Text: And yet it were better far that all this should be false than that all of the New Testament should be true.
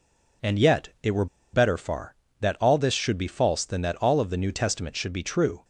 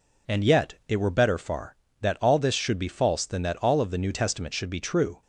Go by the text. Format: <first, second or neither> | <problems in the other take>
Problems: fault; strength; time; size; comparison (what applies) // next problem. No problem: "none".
second | pauses between "were" and "better"; slight; at 1.2 s; 0.27 s long